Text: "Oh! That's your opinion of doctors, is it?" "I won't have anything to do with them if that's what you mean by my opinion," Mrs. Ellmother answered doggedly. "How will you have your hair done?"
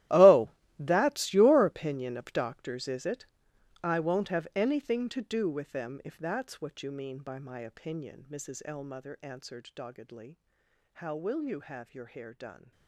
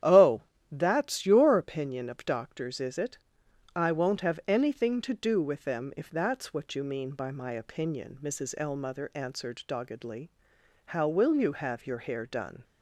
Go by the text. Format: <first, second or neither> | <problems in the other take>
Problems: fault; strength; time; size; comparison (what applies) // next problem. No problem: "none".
second | gets quieter; strong; throughout; 17 dB // starts louder than the rest; strong; until 1.3 s; 14.5 dB; strong in the second